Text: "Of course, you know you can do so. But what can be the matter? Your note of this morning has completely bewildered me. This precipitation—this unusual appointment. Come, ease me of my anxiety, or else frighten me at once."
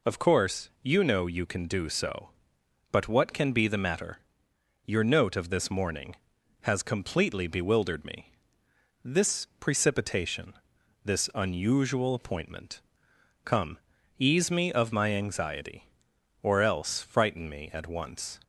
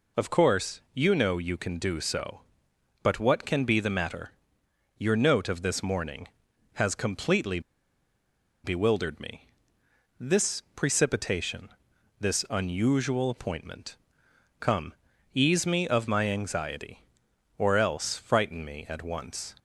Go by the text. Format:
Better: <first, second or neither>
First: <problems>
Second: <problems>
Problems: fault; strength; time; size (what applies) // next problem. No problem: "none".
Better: first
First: none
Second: pauses between "completely" and "bewildered"; at 7.5 s; 1.0 s long